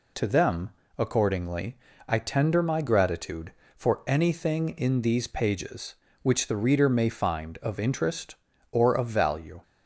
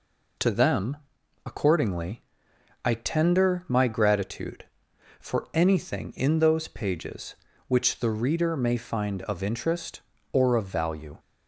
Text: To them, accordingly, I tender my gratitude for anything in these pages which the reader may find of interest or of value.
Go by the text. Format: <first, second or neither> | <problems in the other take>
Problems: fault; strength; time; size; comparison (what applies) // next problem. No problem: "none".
first | says "those" for "these"; at 6.3 s